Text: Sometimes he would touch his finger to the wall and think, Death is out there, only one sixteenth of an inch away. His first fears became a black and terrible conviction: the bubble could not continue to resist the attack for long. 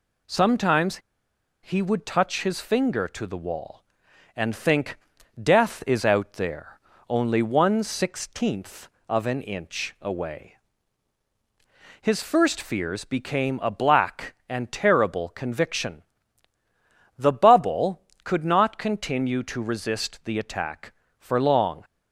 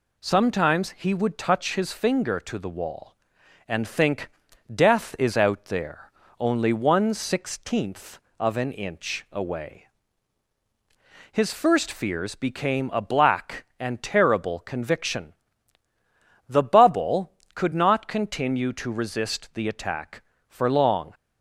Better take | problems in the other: second | pauses between "Sometimes" and "he"; noticeable; at 0.9 s; 0.67 s long

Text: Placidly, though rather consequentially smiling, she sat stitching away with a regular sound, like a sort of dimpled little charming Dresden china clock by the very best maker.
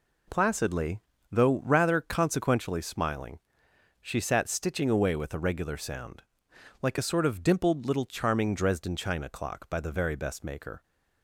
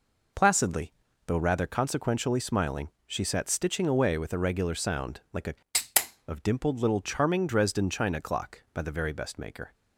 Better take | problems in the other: first | skips "sort"; at 5.8 s

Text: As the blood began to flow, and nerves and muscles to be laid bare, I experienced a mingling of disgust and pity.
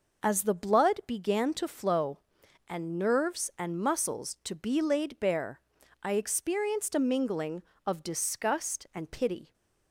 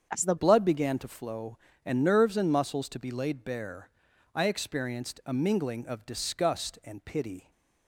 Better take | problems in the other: first | starts louder than the rest; strong; until 1.1 s; 7 dB // changes voice at "blood"; from 0.3 s on; 7.2 s long

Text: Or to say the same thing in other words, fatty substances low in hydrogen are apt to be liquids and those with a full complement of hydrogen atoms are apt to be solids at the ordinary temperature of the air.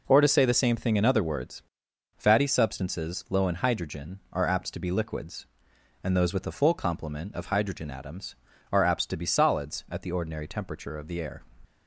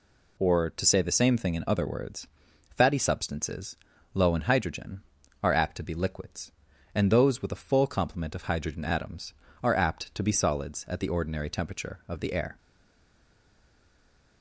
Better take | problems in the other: first | pauses between "substances" and "low"; at 3.7 s; 0.38 s long // stays silent after the last word; noticeable; from 12.5 s on; 1.9 s long

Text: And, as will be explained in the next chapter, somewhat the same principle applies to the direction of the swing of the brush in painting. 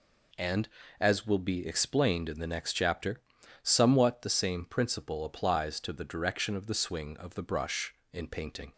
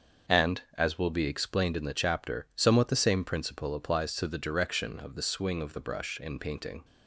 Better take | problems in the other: first | starts louder than the rest; until 1.4 s; 6.5 dB // skips "next"; at 1.9 s

